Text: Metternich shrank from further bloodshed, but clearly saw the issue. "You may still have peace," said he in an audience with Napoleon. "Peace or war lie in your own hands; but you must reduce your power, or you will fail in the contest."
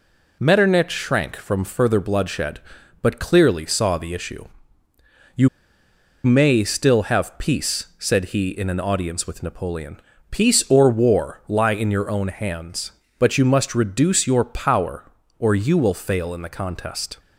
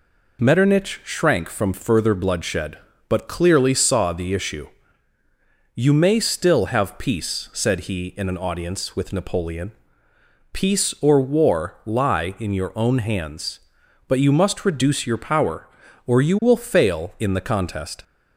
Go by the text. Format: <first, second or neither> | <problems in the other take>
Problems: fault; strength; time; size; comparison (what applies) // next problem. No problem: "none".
second | pauses between "You" and "may"; noticeable; at 5.4 s; 0.76 s long